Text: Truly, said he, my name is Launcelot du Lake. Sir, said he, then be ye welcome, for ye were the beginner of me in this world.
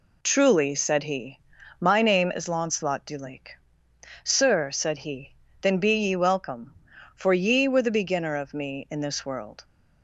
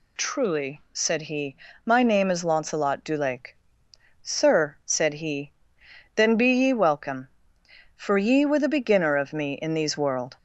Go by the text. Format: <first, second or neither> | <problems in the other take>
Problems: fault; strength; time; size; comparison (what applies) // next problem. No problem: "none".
first | says "these" for "this"; at 9.7 s